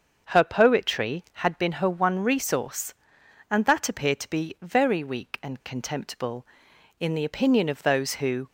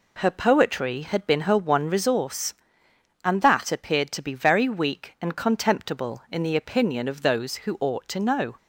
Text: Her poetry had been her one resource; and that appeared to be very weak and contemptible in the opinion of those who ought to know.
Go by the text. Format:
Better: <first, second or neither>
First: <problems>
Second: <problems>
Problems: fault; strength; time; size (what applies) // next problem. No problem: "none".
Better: second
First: starts louder than the rest; until 1.3 s; 6.5 dB // stops before "ought to know"; at 8.4 s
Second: none